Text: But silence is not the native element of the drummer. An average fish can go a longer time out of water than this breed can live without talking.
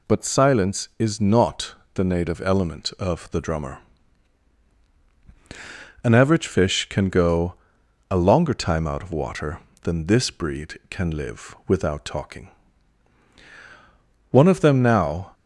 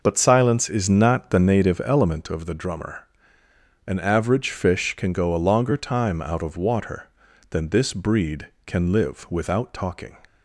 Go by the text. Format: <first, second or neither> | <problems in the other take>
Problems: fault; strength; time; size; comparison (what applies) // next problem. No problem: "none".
second | pauses between "not" and "the"; slight; at 1.7 s; 0.18 s long // pauses between "go" and "a"; noticeable; at 7.5 s; 0.56 s long // goes on to say "One of them now"; noticeable; from 14.3 s on; 1.0 s long